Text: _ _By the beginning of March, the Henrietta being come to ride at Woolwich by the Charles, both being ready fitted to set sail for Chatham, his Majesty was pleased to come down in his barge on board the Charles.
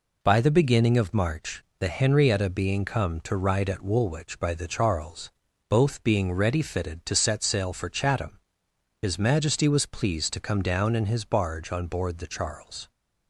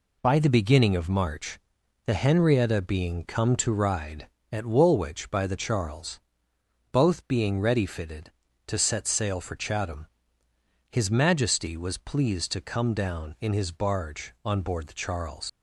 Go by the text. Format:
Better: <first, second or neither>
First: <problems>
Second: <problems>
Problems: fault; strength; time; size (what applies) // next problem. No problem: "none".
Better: first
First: none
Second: leaves "Charles" unfinished; at 15.4 s; 110 ms